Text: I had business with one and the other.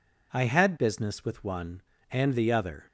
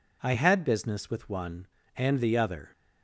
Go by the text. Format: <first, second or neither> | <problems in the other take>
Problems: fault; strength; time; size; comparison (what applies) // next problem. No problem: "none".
neither | none